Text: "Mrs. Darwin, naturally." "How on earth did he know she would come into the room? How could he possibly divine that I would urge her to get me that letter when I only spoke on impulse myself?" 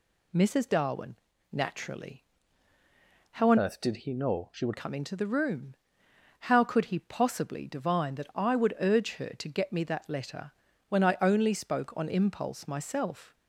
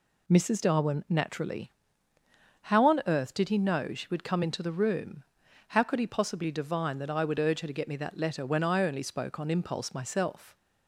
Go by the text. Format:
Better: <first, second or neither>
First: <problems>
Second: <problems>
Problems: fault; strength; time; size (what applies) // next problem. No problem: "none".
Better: second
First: changes voice from "earth" to "would"; from 3.5 to 4.7 s; 1.2 s long // pauses between "letter" and "when"; slight; at 10.5 s; 0.36 s long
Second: none